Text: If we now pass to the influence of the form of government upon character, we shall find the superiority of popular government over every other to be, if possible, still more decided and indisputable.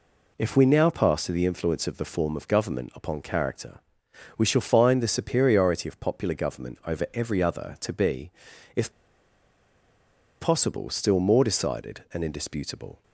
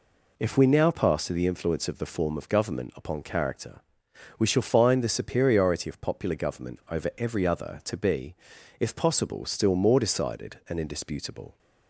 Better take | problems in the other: second | pauses between "if" and "possible"; strong; at 8.9 s; 1.5 s long

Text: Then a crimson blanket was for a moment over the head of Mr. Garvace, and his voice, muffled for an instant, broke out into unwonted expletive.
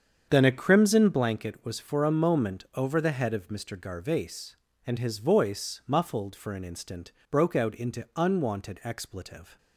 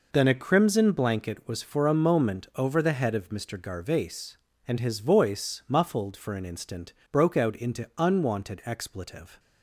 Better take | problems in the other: second | starts louder than the rest; strong; until 1.2 s; 7.5 dB

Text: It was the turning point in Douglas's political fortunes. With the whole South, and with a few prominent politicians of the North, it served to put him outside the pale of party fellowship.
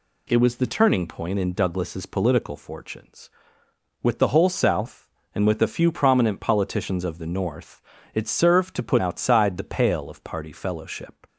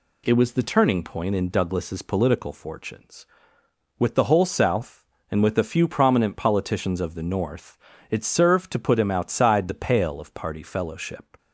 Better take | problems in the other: second | skips "him"; at 8.9 s

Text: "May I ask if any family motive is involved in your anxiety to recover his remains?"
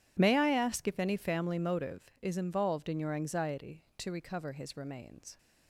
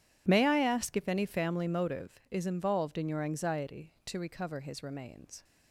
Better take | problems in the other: neither | none

